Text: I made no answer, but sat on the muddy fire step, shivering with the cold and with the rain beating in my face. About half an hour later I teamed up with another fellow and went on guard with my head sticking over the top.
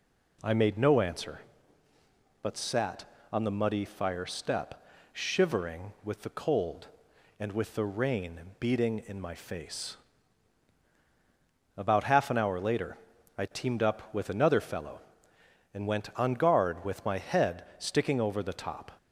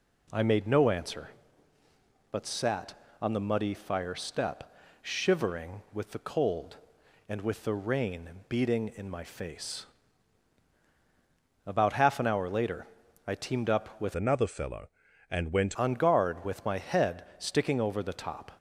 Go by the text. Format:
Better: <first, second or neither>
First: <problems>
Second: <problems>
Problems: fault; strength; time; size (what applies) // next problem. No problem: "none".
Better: first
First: pauses between "rain" and "beating"; slight; at 8.3 s; 0.18 s long // pauses between "later" and "I"; at 12.9 s; 0.40 s long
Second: pauses between "rain" and "beating"; slight; at 8.2 s; 0.18 s long // pauses between "later" and "I"; at 12.8 s; 0.40 s long // changes voice from "another" to "went"; from 14.1 to 15.7 s; 1.6 s long